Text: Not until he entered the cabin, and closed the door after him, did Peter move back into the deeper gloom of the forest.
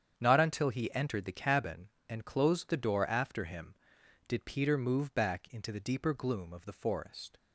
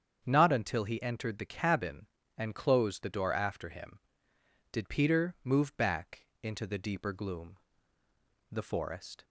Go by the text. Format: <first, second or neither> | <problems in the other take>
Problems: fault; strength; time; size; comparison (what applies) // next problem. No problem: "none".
first | starts louder than the rest; strong; until 1.2 s; 7.5 dB; strong in the first // pauses between "back" and "into"; slight; at 6.2 s; 0.16 s long // skips "of"; at 8.0 s